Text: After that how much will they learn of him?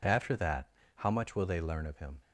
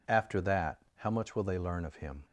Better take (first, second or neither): neither